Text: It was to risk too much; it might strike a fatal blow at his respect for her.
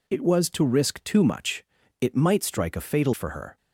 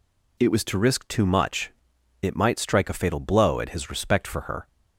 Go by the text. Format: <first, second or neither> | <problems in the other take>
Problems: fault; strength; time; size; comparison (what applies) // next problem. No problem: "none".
second | skips "blow at his respect"; at 3.1 s